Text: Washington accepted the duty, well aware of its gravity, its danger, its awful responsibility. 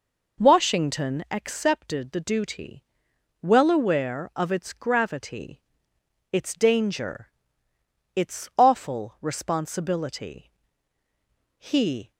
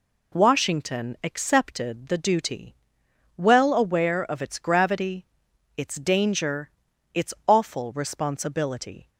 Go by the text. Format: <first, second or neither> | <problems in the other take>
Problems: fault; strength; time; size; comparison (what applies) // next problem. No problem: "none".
second | goes on to say "He"; from 11.5 s on; 0.54 s long